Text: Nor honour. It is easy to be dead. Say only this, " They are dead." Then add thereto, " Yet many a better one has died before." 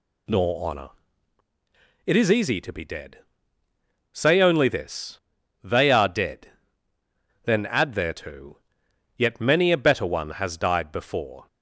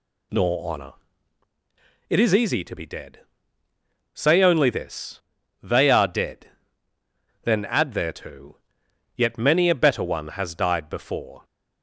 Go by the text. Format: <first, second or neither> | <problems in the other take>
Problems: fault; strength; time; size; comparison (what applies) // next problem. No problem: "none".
neither | none